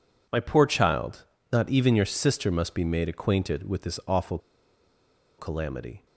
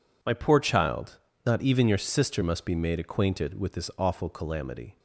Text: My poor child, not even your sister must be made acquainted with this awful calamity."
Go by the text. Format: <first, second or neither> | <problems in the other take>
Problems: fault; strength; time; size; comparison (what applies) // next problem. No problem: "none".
second | pauses between "awful" and "calamity"; at 4.3 s; 1.0 s long